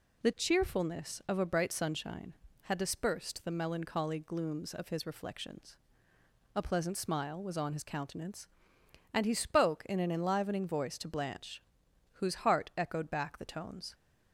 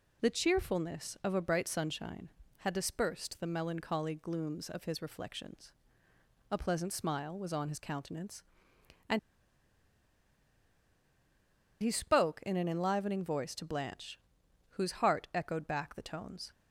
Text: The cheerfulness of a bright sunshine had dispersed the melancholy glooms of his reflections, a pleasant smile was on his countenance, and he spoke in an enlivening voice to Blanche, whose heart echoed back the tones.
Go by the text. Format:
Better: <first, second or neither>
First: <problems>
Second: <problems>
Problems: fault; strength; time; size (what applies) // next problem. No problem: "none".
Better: first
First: none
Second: pauses between "and" and "he"; strong; at 9.1 s; 2.6 s long